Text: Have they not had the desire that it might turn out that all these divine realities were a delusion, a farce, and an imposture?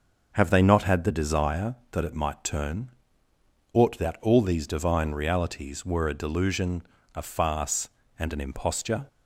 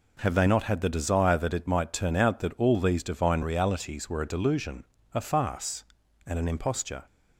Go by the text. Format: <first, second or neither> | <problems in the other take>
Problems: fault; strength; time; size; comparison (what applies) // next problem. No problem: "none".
second | starts louder than the rest; until 1.3 s; 6 dB // says "ought" for "out"; at 3.7 s